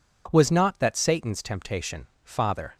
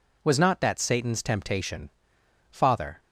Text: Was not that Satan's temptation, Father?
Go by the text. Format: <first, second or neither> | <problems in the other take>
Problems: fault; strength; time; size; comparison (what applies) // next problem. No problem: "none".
neither | none